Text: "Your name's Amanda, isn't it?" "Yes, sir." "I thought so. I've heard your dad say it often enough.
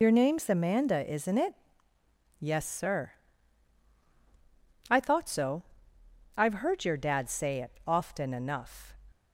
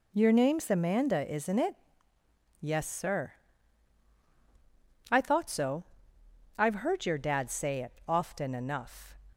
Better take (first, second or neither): second